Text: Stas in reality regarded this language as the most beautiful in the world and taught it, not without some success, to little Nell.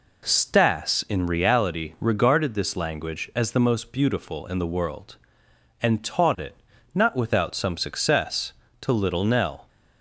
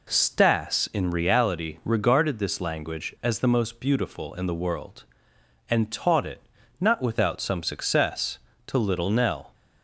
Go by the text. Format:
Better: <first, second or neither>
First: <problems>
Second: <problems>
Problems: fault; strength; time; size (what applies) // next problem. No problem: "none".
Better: neither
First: none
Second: none